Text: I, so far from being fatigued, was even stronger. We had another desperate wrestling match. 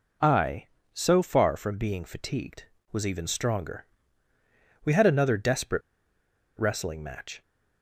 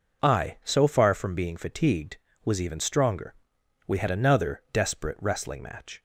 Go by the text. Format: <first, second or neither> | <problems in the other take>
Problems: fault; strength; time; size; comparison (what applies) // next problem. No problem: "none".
second | pauses between "desperate" and "wrestling"; noticeable; at 5.8 s; 0.76 s long